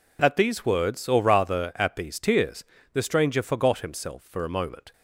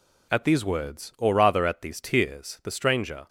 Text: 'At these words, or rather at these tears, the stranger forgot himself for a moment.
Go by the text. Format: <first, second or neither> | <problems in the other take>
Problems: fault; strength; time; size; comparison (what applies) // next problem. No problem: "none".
first | stops before "forgot himself for a moment"; at 3.2 s